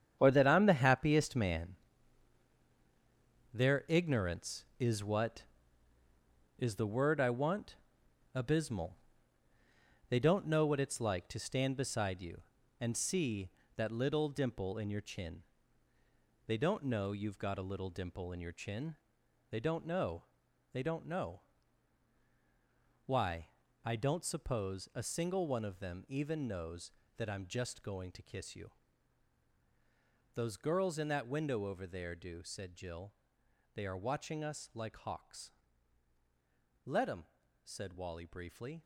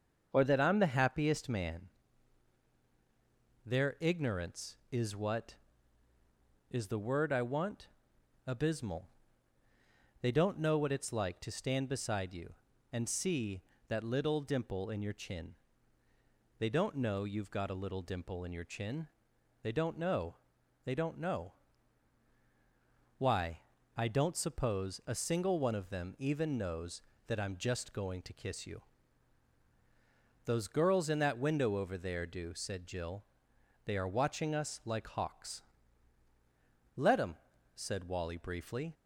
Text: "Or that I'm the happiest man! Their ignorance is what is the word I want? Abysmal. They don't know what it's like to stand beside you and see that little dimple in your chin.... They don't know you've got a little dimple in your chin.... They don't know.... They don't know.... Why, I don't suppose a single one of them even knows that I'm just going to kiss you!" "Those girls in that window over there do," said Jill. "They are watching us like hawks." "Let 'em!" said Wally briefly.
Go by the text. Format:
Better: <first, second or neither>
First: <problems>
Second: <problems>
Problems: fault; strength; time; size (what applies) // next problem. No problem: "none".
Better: second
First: gets quieter; strong; throughout; 10 dB // starts louder than the rest; strong; until 1.1 s; 8.5 dB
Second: starts louder than the rest; until 1.3 s; 6.5 dB